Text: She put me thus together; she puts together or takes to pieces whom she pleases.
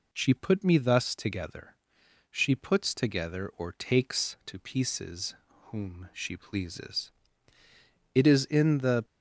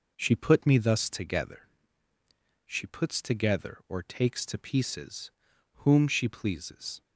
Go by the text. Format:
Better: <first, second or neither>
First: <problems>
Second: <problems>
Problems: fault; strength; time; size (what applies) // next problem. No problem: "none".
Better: second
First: pauses between "pieces" and "whom"; slight; at 5.3 s; 0.34 s long // goes on to say "It is in the"; noticeable; from 8.1 s on; 0.90 s long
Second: pauses between "pieces" and "whom"; at 5.3 s; 0.42 s long